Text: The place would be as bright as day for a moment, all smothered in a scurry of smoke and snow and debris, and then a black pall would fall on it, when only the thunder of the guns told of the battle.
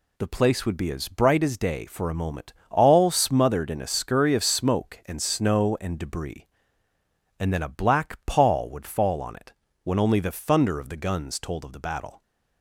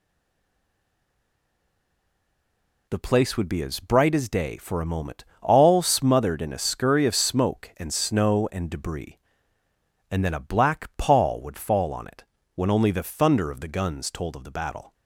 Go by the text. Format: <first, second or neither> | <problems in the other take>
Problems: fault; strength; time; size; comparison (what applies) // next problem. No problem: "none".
first | stays silent before the first word; strong; until 2.8 s; 2.8 s long